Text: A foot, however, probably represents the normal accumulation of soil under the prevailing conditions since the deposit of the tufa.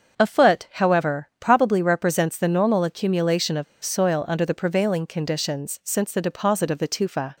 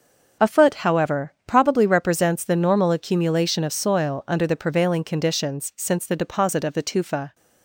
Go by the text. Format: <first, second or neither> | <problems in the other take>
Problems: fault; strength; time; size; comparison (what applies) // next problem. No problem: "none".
second | starts louder than the rest; until 1.2 s; 6.5 dB; strong in the second // pauses between "of" and "soil"; slight; at 3.6 s; 0.19 s long